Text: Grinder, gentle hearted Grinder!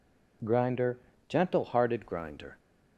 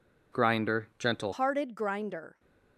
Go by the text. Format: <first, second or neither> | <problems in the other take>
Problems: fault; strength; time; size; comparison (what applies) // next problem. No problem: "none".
first | changes voice at "hearted"; from 1.3 s on; 1.0 s long